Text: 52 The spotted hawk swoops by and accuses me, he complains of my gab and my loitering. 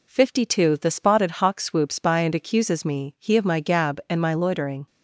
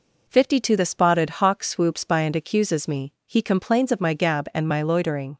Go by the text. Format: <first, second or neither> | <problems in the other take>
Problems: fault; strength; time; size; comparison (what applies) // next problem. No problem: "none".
second | skips "complains"; at 3.3 s